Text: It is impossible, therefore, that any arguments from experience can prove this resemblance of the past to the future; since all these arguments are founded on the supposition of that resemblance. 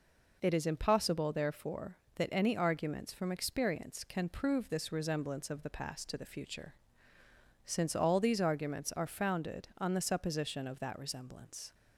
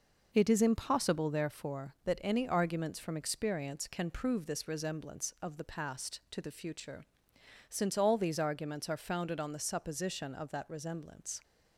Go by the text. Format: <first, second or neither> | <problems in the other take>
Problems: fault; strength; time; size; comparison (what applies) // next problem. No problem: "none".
neither | none